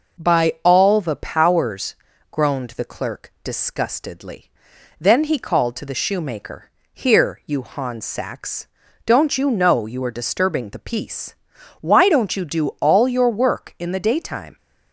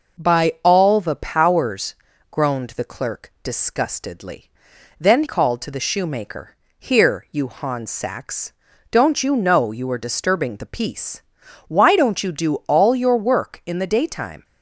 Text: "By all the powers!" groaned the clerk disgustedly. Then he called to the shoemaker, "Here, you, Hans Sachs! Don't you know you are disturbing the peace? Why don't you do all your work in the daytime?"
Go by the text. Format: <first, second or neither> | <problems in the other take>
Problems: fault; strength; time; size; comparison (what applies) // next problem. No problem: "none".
first | skips "he"; at 5.2 s